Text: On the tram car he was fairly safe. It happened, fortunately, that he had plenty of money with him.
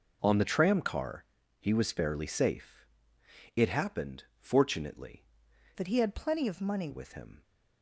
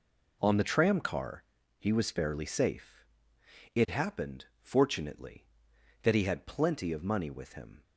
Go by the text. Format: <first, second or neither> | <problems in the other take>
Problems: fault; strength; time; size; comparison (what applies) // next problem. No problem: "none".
second | pauses between "car" and "he"; slight; at 1.2 s; 0.34 s long; slight in the second // changes voice from "that" to "money"; from 5.7 to 6.8 s; 1.1 s long